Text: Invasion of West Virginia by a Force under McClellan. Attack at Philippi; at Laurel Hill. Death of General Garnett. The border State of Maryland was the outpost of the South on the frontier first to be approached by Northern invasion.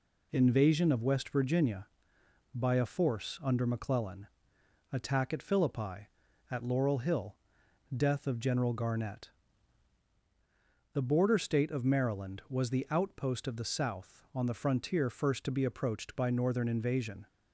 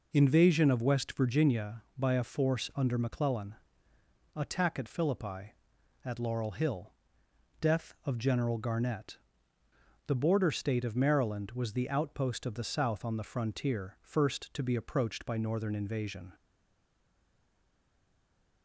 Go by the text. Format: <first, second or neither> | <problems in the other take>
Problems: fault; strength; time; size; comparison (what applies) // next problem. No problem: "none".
first | stays silent after the last word; from 16.3 s on; 2.3 s long